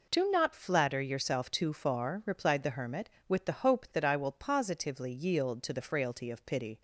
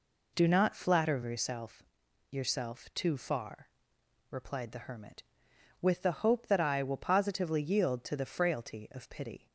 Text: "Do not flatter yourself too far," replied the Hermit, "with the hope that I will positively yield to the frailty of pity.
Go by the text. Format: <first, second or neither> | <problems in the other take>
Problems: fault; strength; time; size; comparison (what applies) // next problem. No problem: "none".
first | says "yourself" twice; at 2.3 s